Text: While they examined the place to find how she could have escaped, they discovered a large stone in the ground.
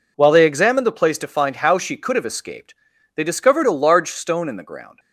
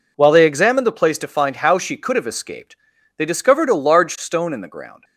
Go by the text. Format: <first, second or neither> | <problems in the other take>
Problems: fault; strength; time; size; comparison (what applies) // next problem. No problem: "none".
neither | none